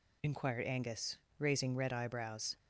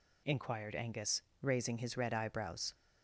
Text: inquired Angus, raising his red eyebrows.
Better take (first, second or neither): second